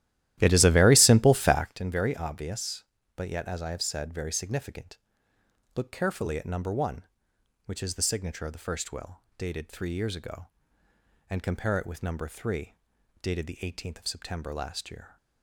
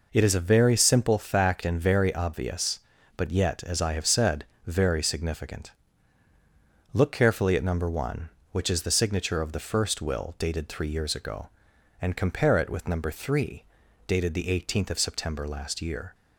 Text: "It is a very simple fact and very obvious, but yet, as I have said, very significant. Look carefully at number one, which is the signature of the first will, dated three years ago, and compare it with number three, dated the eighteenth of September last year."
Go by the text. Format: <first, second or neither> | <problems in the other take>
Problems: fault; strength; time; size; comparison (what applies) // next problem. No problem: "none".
second | starts louder than the rest; strong; until 1.8 s; 13.5 dB